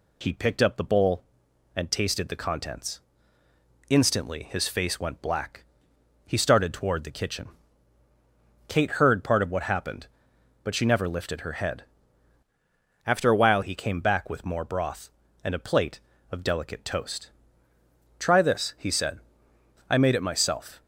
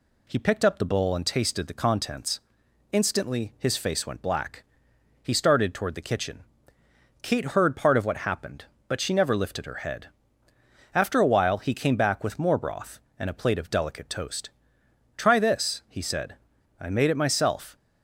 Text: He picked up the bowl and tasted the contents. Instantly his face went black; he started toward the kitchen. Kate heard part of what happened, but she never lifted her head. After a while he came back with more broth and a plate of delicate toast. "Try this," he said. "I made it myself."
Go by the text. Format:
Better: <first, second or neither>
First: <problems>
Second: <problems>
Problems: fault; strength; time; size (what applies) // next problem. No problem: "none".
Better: second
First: changes voice from "After" to "while"; from 13.0 to 13.6 s; 0.6 s long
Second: none